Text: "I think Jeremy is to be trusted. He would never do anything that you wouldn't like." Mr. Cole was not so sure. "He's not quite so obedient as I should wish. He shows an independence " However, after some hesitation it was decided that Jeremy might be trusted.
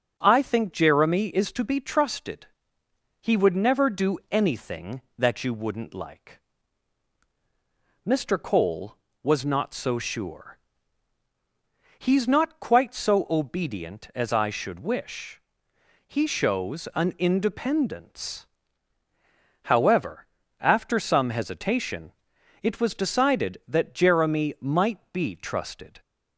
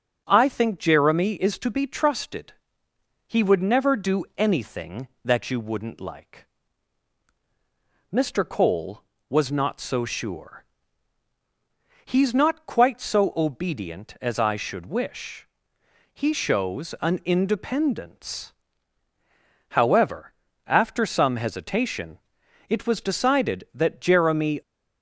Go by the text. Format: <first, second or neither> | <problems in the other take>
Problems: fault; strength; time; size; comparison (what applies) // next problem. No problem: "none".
first | starts louder than the rest; until 1.2 s; 7 dB; also in the first // pauses between "hesitation" and "it"; noticeable; at 22.1 s; 0.52 s long; noticeable in the first // stops before "might be trusted"; at 24.6 s